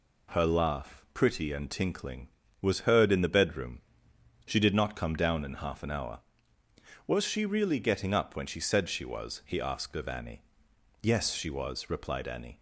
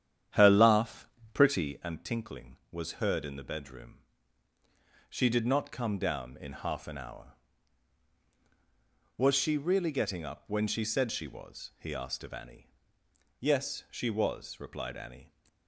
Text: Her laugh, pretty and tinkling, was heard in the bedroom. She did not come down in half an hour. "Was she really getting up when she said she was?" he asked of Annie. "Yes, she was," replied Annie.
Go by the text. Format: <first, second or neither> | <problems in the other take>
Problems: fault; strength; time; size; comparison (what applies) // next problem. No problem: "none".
first | starts louder than the rest; strong; until 2.0 s; 10 dB